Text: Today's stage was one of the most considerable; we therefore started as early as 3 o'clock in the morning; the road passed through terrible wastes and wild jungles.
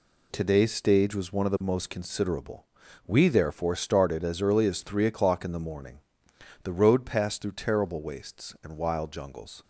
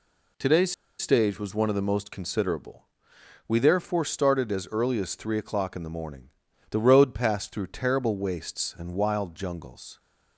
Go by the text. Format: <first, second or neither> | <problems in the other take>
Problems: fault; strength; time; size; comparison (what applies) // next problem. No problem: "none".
first | pauses between "Today's" and "stage"; slight; at 0.7 s; 0.26 s long